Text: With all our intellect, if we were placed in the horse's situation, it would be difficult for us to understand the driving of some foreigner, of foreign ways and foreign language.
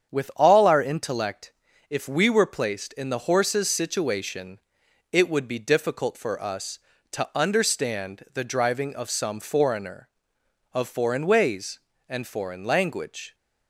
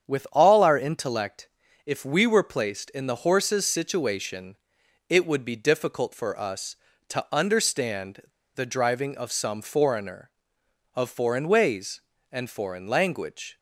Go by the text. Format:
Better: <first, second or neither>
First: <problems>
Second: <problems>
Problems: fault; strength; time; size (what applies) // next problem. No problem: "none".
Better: first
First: starts louder than the rest; strong; until 1.1 s; 8 dB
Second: starts louder than the rest; strong; until 1.1 s; 8 dB // pauses between "understand" and "the"; slight; at 8.2 s; 0.32 s long